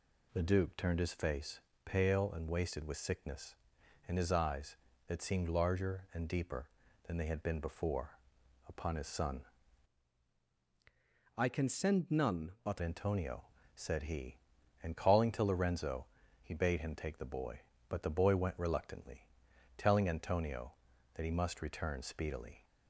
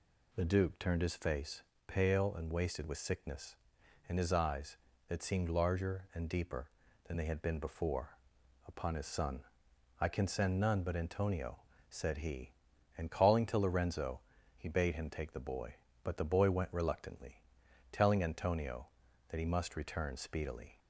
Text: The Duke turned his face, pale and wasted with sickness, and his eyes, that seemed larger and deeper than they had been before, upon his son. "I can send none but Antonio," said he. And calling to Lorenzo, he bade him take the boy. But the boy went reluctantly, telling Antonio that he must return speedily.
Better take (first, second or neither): second